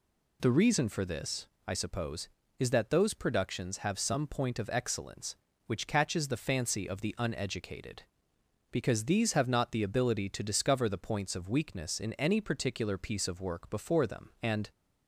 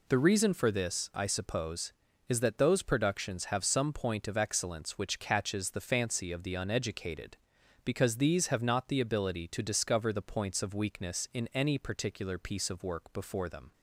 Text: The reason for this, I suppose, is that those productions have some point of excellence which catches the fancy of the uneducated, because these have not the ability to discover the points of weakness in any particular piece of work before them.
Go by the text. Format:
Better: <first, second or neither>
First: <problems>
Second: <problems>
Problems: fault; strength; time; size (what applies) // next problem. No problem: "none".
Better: second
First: goes on to say "And"; slight; from 14.4 s on; 0.28 s long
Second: none